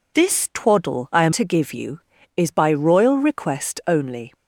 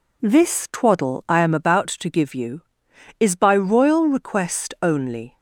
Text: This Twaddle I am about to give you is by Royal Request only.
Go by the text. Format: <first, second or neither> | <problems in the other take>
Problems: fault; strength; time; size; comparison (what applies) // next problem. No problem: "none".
second | skips "about"; at 1.3 s